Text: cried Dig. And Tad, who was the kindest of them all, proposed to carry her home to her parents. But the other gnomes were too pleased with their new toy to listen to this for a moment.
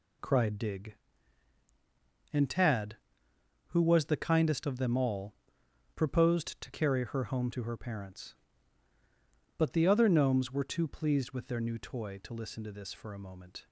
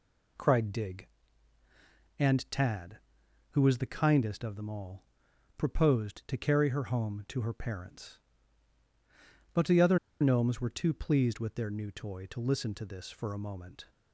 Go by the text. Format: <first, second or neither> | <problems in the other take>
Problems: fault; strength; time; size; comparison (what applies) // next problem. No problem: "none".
first | pauses between "other" and "gnomes"; slight; at 9.9 s; 0.22 s long